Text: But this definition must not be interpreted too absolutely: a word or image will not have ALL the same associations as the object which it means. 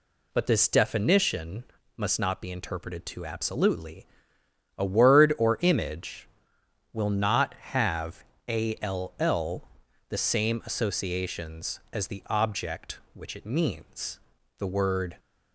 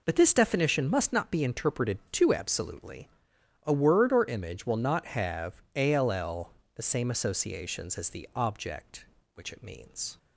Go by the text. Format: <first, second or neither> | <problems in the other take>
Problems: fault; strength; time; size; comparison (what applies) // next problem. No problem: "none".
second | pauses between "definition" and "must"; slight; at 1.6 s; 0.32 s long // pauses between "have" and "ALL"; slight; at 8.2 s; 0.26 s long // pauses between "ALL" and "the"; at 9.6 s; 0.42 s long; slight in the second // goes on to say "The word"; from 14.5 s on; 0.58 s long